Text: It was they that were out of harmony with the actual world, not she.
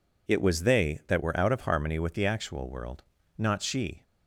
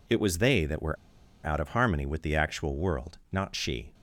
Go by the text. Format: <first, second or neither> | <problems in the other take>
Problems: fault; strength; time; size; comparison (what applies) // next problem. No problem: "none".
first | pauses between "were" and "out"; noticeable; at 0.9 s; 0.49 s long